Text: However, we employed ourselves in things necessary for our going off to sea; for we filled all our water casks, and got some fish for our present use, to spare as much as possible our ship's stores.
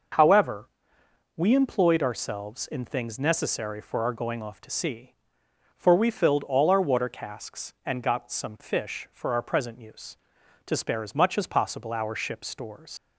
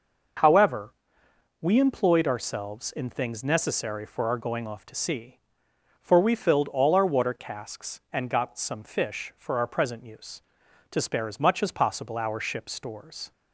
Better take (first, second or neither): second